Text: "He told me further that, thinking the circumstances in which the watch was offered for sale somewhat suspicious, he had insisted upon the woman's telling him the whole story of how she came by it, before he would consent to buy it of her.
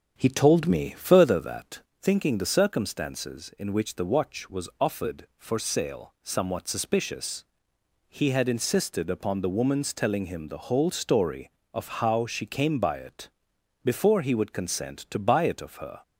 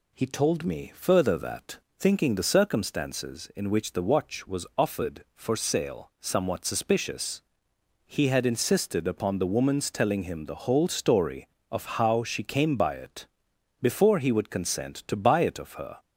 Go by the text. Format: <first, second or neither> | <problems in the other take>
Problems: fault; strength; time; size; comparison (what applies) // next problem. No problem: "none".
second | starts louder than the rest; strong; until 1.4 s; 7.5 dB